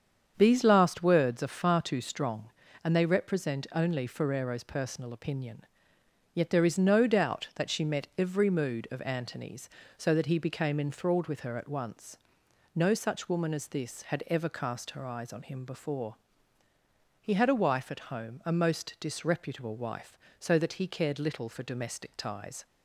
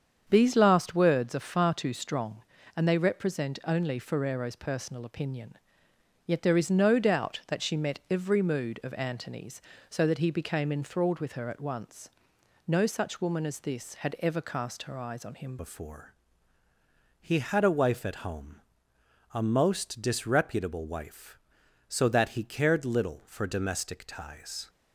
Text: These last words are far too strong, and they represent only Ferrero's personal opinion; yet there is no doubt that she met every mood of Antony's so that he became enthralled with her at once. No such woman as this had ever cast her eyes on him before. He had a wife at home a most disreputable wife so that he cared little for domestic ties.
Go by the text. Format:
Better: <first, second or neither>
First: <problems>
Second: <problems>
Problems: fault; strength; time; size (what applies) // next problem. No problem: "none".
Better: first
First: starts louder than the rest; strong; until 1.3 s; 7.5 dB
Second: starts louder than the rest; strong; until 1.2 s; 7.5 dB // changes voice at "before"; from 15.5 s on; 9.1 s long // pauses between "home" and "a"; noticeable; at 18.6 s; 0.72 s long